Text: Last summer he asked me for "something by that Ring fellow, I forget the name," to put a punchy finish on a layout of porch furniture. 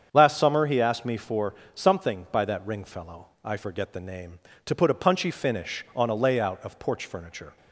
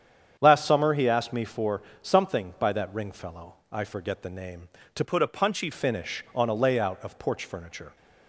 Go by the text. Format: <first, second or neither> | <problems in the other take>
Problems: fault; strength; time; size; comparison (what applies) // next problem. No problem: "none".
first | starts louder than the rest; strong; until 1.4 s; 8.5 dB; strong in the first // pauses between "for" and "something"; slight; at 1.8 s; 0.22 s long; slight in the first // changes voice from "put" to "punchy"; from 5.0 to 5.6 s; 0.6 s long